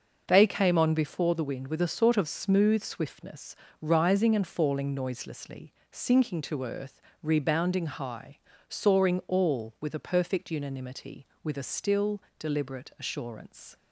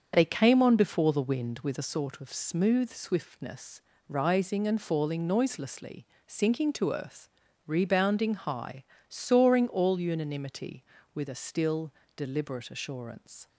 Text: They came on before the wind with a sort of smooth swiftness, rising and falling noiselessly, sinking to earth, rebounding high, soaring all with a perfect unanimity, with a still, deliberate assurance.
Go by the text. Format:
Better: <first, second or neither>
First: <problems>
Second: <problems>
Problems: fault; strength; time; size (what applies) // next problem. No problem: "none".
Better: first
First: starts louder than the rest; noticeable; until 1.2 s; 6 dB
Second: starts louder than the rest; until 1.1 s; 7 dB // skips "with a perfect"; at 9.9 s